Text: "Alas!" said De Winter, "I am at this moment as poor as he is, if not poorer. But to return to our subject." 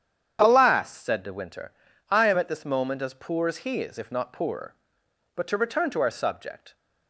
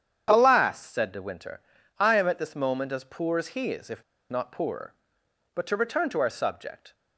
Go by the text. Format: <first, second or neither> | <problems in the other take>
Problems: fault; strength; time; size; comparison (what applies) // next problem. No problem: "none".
first | starts louder than the rest; strong; until 1.3 s; 8.5 dB; strong in the first // pauses between "if" and "not"; slight; at 4.0 s; 0.27 s long